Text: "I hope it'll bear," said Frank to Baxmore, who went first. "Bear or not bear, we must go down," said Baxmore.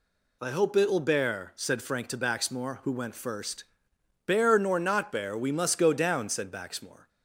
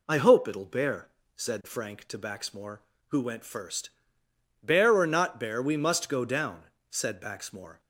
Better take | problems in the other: second | says "nor" for "or"; at 4.5 s

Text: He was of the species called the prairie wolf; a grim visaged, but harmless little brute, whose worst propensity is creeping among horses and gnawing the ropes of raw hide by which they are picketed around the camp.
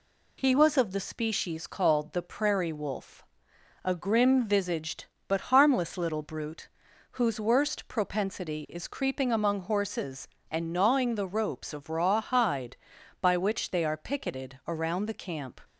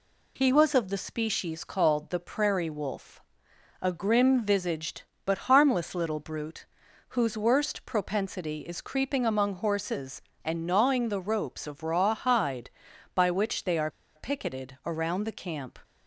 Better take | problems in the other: first | pauses between "are" and "picketed"; slight; at 13.8 s; 0.27 s long

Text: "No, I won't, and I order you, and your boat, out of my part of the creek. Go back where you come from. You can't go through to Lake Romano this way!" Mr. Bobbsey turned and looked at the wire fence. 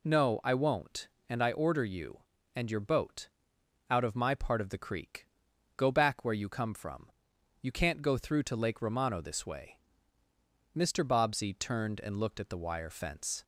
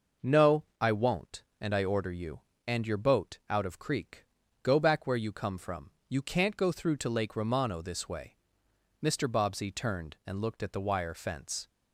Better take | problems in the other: first | skips "my part of the"; at 3.7 s

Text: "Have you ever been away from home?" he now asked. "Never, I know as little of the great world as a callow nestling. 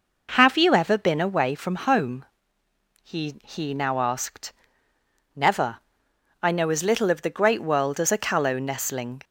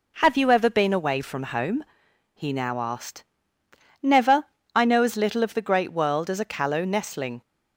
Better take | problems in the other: second | says "he" twice; at 3.4 s

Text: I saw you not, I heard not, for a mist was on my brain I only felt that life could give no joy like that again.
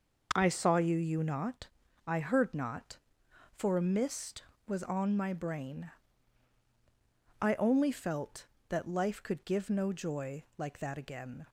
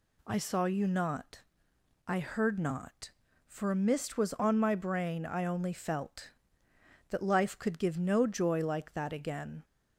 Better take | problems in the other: second | says "you" twice; at 0.9 s // pauses between "brain" and "I"; strong; at 5.9 s; 1.5 s long

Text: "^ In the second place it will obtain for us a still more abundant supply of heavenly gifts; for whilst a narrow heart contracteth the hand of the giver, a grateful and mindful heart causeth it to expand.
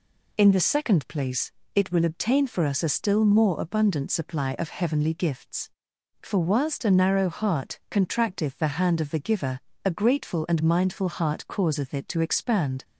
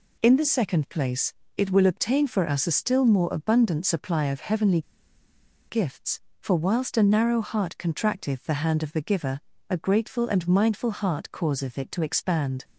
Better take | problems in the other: first | pauses between "place" and "it"; slight; at 1.3 s; 0.22 s long; slight in the first // pauses between "heavenly" and "gifts"; noticeable; at 4.8 s; 0.87 s long

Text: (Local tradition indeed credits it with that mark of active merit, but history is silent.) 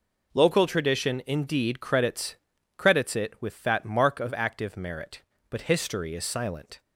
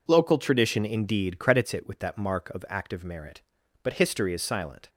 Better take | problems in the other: second | says "credits" twice; at 2.7 s

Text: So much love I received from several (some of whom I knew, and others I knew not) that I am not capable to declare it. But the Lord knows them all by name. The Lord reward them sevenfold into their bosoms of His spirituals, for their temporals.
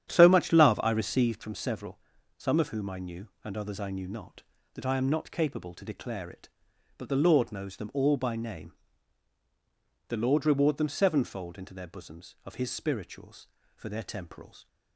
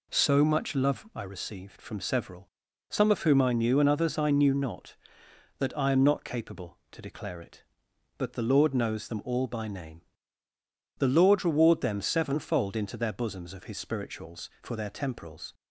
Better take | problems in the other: second | starts louder than the rest; strong; until 1.4 s; 10 dB

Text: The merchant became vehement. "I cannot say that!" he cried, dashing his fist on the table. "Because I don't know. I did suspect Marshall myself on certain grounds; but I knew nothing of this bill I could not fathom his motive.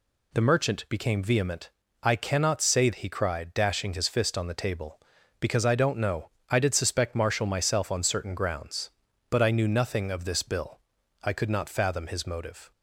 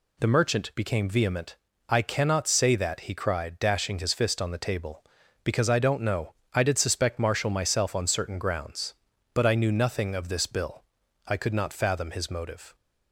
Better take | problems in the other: second | skips "that"; at 2.9 s // pauses between "bill" and "I"; at 10.7 s; 0.44 s long; also in the second

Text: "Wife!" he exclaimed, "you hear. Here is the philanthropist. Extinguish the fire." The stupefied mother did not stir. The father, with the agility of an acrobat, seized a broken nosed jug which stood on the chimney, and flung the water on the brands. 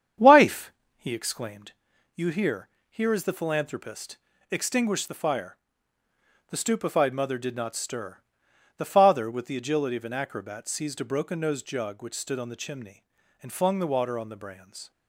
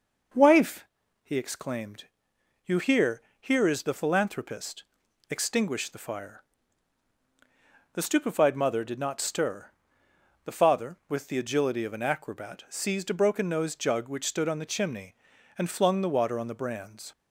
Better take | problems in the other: second | starts louder than the rest; strong; until 1.6 s; 8.5 dB

